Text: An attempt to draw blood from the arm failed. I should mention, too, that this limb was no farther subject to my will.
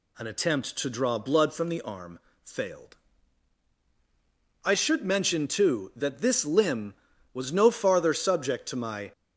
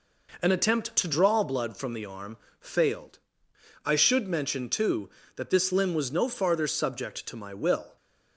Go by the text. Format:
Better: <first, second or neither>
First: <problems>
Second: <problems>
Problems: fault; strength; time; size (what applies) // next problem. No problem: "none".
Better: second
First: pauses between "arm" and "failed"; slight; at 2.1 s; 0.22 s long // stops before "will"; at 9.1 s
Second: pauses between "arm" and "failed"; slight; at 2.3 s; 0.22 s long